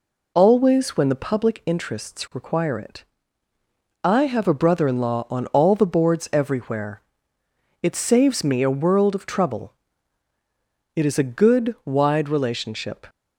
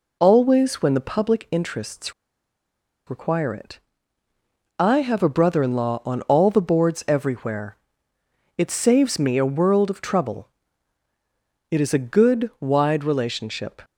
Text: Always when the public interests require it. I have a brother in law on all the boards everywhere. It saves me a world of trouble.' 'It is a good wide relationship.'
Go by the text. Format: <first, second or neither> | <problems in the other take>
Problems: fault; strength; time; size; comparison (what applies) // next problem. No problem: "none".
first | pauses between "interests" and "require"; noticeable; at 2.1 s; 0.95 s long